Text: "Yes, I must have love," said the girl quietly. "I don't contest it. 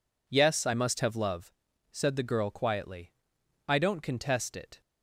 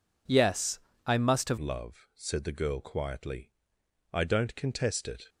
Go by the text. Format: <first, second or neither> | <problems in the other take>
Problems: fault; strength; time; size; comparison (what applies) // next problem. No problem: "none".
first | changes voice at "love"; from 1.5 s on; 3.7 s long